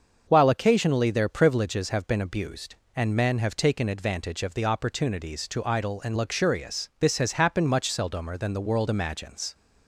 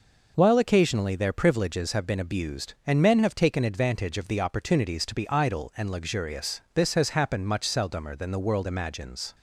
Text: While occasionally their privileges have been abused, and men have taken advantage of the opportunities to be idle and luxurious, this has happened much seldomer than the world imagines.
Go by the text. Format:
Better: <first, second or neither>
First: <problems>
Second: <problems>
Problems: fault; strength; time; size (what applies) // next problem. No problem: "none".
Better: second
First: starts louder than the rest; until 1.3 s; 6.5 dB // skips "be"; at 5.6 s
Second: none